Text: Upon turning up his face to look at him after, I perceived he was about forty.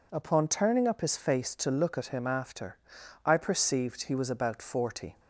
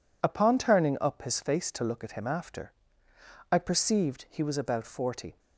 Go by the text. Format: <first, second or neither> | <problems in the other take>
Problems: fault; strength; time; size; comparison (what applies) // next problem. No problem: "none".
neither | none